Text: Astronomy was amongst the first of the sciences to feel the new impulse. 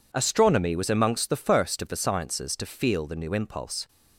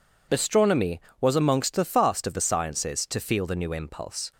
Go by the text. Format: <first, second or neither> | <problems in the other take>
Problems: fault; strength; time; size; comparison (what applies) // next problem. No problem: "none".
first | says "fast" for "first"; at 1.8 s